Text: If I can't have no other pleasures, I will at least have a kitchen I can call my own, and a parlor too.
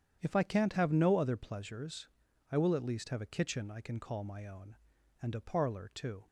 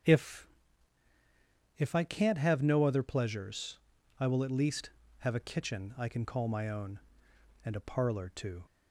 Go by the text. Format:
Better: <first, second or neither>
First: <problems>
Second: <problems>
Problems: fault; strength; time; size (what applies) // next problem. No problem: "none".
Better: first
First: starts louder than the rest; strong; until 1.2 s; 9 dB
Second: starts louder than the rest; strong; until 2.3 s; 7.5 dB // says "If" twice; at 1.7 s